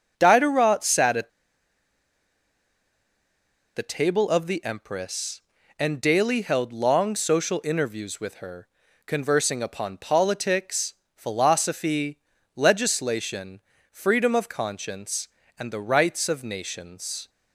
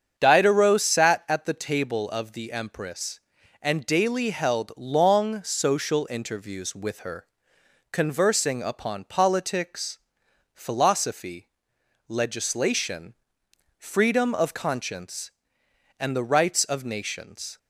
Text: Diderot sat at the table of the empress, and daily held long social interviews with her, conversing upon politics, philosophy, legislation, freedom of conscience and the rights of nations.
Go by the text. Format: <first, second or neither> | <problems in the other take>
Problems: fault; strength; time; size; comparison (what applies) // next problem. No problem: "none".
second | starts louder than the rest; until 1.1 s; 6.5 dB; strong in the second // pauses between "at" and "the"; strong; at 1.2 s; 2.4 s long